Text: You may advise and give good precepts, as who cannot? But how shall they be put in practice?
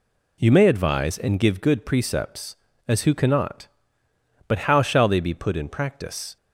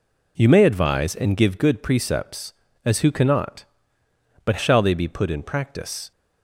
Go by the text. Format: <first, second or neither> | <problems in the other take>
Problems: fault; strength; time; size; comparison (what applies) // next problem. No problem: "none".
first | skips "how"; at 4.5 s